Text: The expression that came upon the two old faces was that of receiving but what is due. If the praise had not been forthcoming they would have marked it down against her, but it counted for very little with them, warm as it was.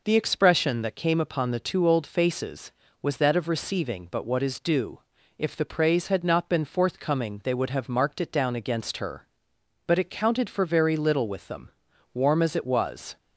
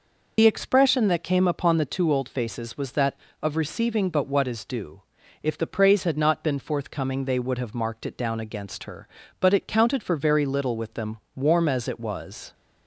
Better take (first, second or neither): first